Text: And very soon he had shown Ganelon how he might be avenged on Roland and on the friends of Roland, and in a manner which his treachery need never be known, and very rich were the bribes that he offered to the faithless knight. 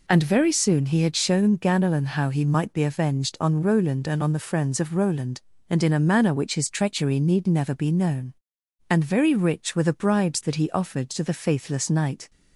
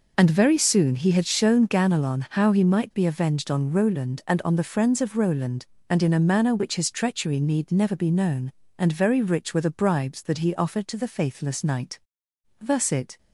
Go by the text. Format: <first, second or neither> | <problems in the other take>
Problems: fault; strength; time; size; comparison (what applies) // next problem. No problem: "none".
first | goes on to say "Thus it"; from 12.5 s on; 0.58 s long